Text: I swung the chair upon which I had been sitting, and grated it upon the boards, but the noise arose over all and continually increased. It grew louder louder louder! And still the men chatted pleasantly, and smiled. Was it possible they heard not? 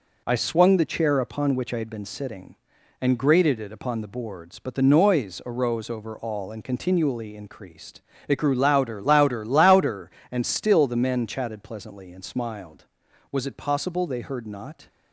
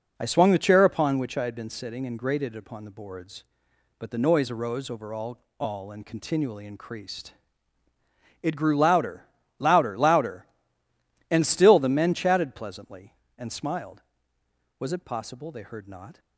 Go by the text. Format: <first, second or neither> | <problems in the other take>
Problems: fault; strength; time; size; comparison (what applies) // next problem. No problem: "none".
first | says "all" twice; at 5.5 s // pauses between "louder" and "louder"; slight; at 9.2 s; 0.34 s long